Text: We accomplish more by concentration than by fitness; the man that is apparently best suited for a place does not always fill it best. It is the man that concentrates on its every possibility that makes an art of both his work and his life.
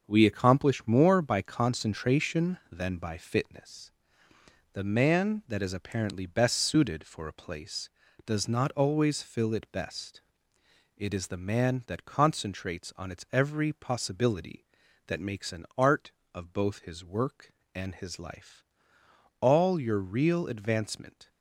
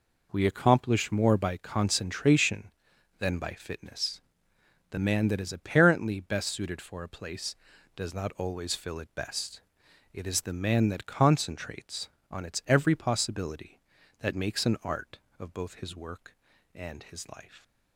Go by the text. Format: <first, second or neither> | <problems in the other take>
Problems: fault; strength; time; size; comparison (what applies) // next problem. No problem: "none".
second | starts louder than the rest; until 1.0 s; 6.5 dB // goes on to say "All your real advancement"; strong; from 19.4 s on; 1.8 s long